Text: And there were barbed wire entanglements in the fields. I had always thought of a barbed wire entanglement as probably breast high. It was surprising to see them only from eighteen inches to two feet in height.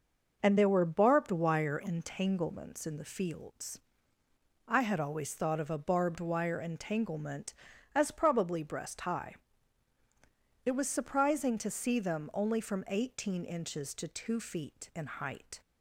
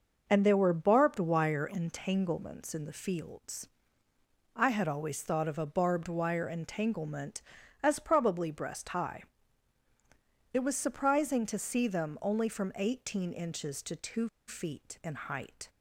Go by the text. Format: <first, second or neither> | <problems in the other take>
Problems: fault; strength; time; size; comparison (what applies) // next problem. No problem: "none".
first | pauses between "two" and "feet"; slight; at 14.2 s; 0.19 s long